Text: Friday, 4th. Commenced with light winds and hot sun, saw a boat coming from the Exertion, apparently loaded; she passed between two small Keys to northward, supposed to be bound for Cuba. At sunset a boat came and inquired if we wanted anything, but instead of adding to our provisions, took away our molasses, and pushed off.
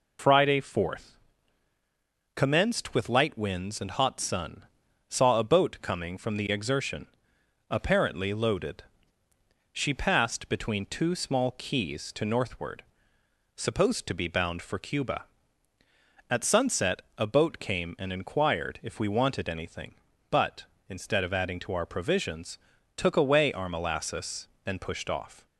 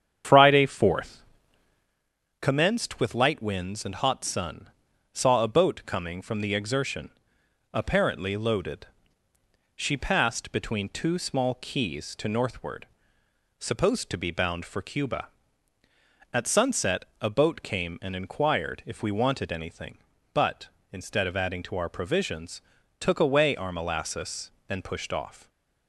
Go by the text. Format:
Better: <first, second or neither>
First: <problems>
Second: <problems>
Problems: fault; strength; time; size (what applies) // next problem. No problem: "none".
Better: first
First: pauses between "sunset" and "a"; slight; at 17.0 s; 0.16 s long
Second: starts louder than the rest; strong; until 2.1 s; 8.5 dB // pauses between "sunset" and "a"; slight; at 17.0 s; 0.16 s long